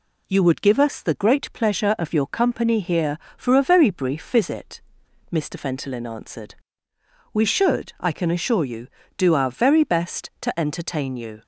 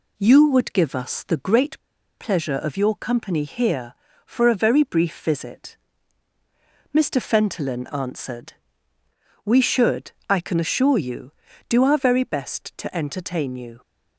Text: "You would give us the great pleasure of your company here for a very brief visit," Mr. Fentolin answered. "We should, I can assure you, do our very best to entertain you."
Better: first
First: none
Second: pauses between "great" and "pleasure"; at 1.7 s; 0.41 s long

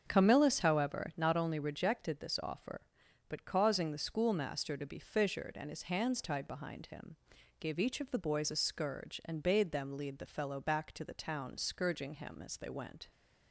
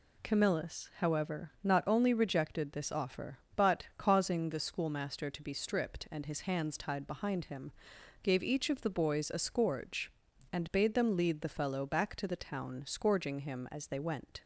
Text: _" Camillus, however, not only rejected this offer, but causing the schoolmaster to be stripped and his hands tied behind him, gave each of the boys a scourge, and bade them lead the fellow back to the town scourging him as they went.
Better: second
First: starts louder than the rest; until 1.0 s; 7 dB // says "fissured" for "stripped"; at 4.9 s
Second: none

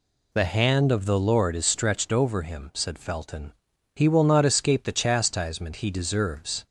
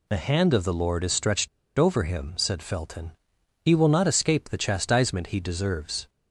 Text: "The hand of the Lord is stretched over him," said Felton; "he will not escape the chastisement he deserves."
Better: first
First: none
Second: pauses between "stretched" and "over"; slight; at 1.4 s; 0.30 s long

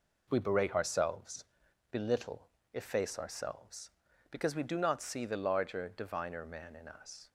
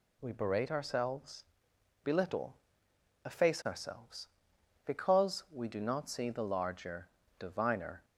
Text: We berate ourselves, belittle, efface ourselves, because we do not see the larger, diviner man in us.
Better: first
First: none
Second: stops before "man in us"; at 8.0 s

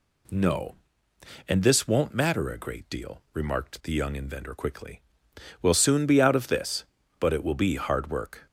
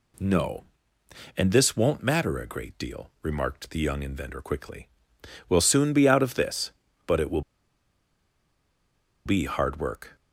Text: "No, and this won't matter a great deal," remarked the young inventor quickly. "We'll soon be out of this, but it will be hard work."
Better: first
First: none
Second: pauses between "will" and "be"; strong; at 7.4 s; 1.8 s long

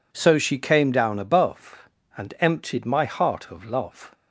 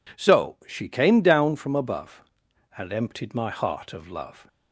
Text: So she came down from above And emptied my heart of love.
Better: second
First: skips "from"; at 1.2 s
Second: none

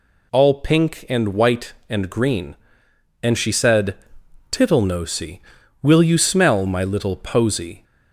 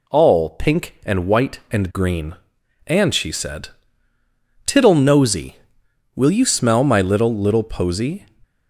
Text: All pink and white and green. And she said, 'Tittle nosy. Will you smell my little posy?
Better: first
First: none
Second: says "little" twice; at 7.3 s

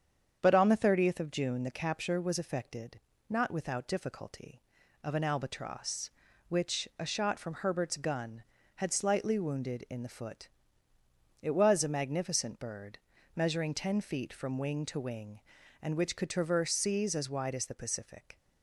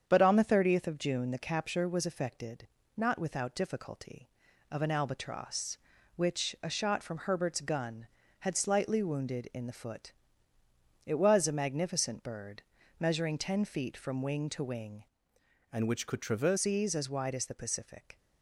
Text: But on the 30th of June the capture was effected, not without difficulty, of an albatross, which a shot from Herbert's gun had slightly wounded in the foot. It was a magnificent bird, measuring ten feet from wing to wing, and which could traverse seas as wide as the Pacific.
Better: first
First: starts louder than the rest; strong; until 1.4 s; 7.5 dB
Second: starts louder than the rest; strong; until 1.0 s; 7.5 dB // changes voice from "and" to "traverse"; from 15.7 to 16.5 s; 0.8 s long

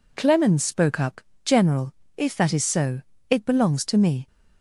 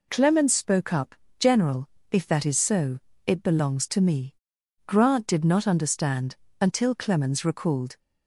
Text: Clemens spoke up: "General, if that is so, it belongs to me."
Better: first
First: none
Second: goes on to say "Grant did not understand until Clemens recalled"; strong; from 4.8 s on; 3.1 s long

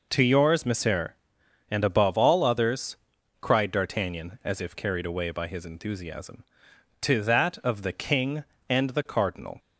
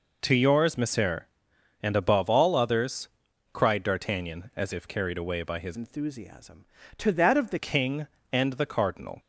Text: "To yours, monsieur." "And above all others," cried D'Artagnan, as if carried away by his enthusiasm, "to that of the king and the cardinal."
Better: first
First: none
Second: changes voice from "enthusiasm" to "the"; from 5.7 to 7.5 s; 1.8 s long

